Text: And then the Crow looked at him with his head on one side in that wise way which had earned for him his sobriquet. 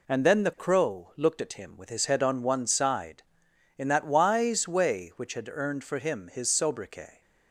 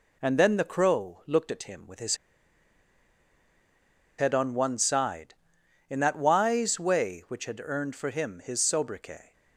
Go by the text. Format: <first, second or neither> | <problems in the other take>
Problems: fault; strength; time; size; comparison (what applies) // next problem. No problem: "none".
first | pauses between "his" and "head"; strong; at 2.1 s; 2.0 s long